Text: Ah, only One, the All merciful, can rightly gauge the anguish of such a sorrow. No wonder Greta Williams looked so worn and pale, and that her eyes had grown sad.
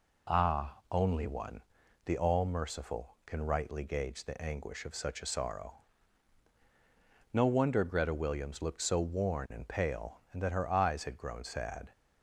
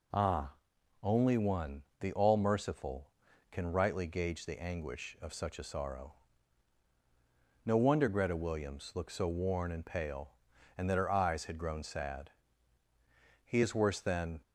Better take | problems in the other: first | goes on to say "He is worse than"; noticeable; from 13.4 s on; 0.92 s long

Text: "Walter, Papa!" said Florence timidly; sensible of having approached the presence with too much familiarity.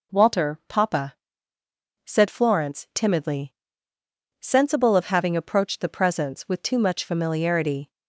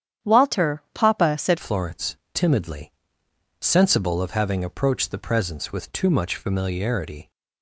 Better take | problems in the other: first | starts louder than the rest; strong; until 1.3 s; 9.5 dB // changes voice at "Florence"; from 1.5 s on; 5.8 s long // pauses between "Florence" and "timidly"; slight; at 2.1 s; 0.18 s long

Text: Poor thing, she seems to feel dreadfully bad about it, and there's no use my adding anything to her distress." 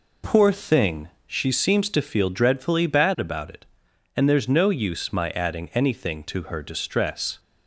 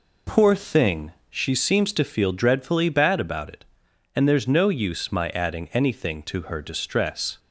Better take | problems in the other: neither | none

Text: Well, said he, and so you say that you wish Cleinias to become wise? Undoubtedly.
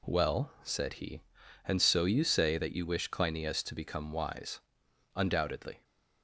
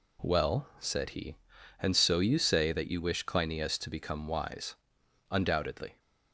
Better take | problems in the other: neither | none

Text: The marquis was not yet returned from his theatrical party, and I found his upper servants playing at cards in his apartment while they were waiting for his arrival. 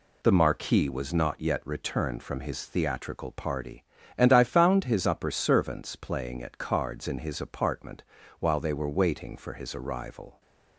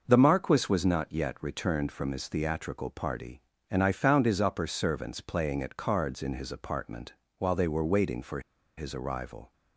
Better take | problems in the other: first | pauses between "apartment" and "while"; slight; at 7.1 s; 0.26 s long; slight in the first // pauses between "for" and "his"; at 8.4 s; 0.36 s long

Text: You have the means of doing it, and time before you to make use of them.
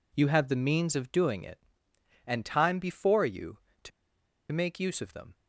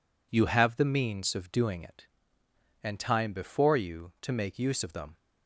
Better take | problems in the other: second | pauses between "to" and "make"; noticeable; at 3.9 s; 0.62 s long

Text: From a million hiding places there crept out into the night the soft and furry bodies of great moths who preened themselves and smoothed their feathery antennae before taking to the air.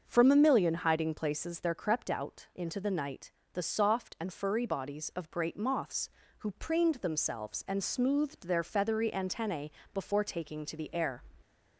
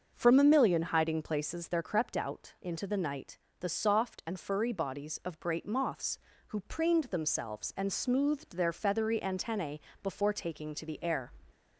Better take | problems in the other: neither | starts louder than the rest; the same in both // pauses between "night" and "the"; slight; the same in both // pauses between "antennae" and "before"; slight; the same in both

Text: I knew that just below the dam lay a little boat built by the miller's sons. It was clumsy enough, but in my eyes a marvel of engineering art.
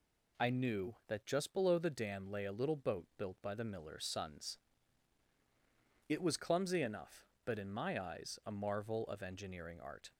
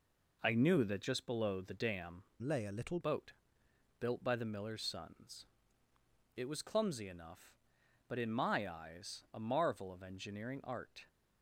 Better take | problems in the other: first | changes voice from "lay" to "little"; from 2.4 to 2.9 s; 0.5 s long // pauses between "boat" and "built"; noticeable; at 3.3 s; 0.68 s long

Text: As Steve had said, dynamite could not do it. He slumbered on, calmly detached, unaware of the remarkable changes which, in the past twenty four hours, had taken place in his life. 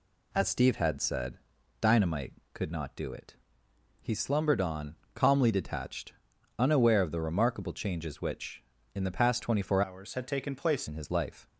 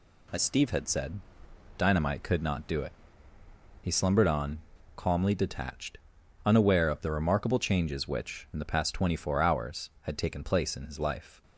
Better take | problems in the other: second | changes voice from "hours" to "place"; from 9.8 to 10.8 s; 1.0 s long

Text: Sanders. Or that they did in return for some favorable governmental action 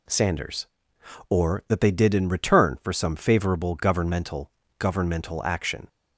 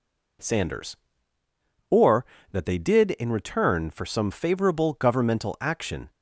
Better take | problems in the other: second | says "governmental" twice; at 4.7 s

